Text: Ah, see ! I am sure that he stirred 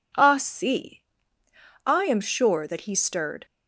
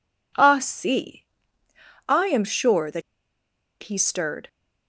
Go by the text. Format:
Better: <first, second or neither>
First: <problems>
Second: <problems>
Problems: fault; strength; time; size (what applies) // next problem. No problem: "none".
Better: first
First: none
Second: pauses between "that" and "he"; noticeable; at 3.0 s; 0.81 s long